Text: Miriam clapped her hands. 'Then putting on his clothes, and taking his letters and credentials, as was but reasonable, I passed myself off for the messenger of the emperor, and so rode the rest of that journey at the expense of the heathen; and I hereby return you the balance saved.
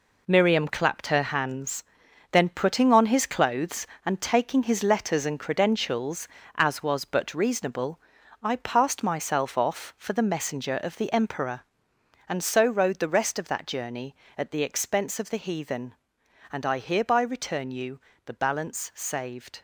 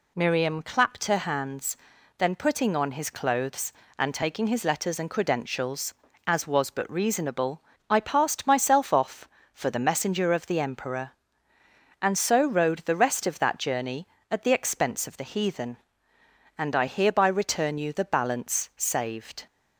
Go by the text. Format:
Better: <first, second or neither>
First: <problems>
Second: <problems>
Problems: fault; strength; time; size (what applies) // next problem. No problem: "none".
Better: second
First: gets quieter; strong; throughout; 8.5 dB // pauses between "you" and "the"; slight; at 17.9 s; 0.24 s long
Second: none